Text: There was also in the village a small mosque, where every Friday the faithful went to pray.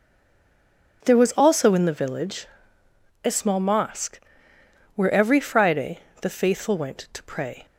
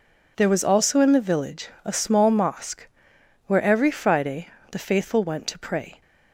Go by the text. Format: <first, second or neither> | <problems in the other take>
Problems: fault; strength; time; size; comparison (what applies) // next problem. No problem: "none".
second | stays silent before the first word; until 1.0 s; 1.0 s long // pauses between "village" and "a"; noticeable; at 2.4 s; 0.78 s long; slight in the second // pauses between "Friday" and "the"; slight; at 5.9 s; 0.24 s long; slight in the second